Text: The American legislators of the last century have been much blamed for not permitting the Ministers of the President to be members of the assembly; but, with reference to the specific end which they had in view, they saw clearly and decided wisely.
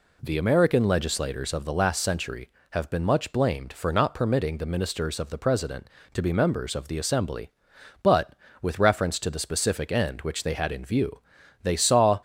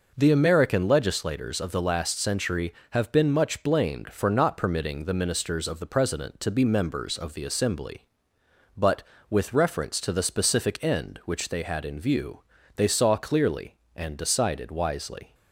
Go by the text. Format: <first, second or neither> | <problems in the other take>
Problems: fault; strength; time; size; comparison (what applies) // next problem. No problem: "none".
second | stops before "clearly and decided wisely"; at 12.1 s